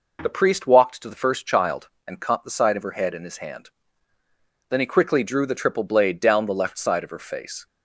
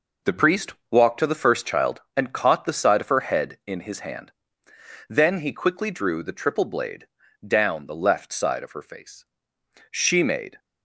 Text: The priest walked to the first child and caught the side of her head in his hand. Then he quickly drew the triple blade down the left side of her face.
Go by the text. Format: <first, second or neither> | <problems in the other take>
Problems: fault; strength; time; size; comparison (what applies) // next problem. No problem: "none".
first | pauses between "priest" and "walked"; slight; at 0.7 s; 0.18 s long // pauses between "blade" and "down"; at 7.0 s; 0.38 s long // goes on to say "She made"; noticeable; from 9.9 s on; 0.68 s long